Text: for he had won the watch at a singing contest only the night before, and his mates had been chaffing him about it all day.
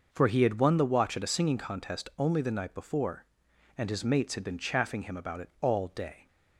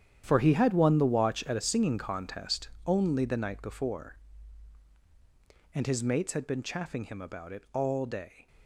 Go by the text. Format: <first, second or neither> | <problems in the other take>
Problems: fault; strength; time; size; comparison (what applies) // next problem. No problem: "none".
first | gets quieter; strong; throughout; 12 dB // pauses between "contest" and "only"; slight; at 2.6 s; 0.18 s long